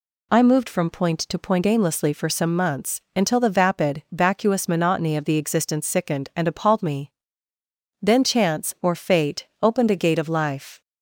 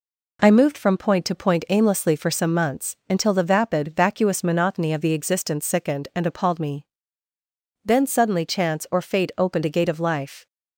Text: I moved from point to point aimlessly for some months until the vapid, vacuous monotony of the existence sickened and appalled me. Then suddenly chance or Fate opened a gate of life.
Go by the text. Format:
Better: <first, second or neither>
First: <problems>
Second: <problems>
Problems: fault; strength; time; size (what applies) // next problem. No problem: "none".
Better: second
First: skips "suddenly"; at 8.2 s // pauses between "Fate" and "opened"; slight; at 9.4 s; 0.16 s long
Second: none